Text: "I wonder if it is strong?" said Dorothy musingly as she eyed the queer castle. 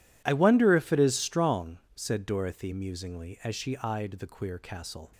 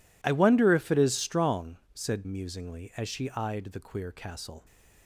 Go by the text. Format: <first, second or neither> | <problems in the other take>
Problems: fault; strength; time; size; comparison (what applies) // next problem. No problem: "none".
first | skips "Dorothy"; at 2.2 s